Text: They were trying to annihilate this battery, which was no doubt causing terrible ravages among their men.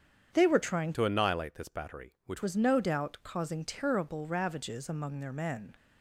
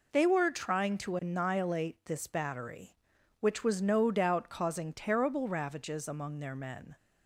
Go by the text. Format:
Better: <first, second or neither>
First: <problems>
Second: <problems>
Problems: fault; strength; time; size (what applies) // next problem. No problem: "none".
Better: second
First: starts louder than the rest; strong; until 1.3 s; 8 dB // changes voice from "to" to "which"; from 0.9 to 2.4 s; 1.5 s long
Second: none